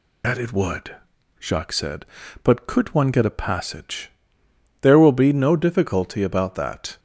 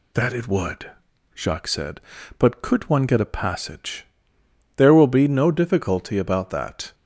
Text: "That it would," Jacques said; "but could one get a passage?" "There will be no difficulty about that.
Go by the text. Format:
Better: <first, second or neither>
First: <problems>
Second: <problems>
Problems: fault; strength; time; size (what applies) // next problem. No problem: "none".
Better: second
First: loses the start of "That"; at 0.2 s; 55 ms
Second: none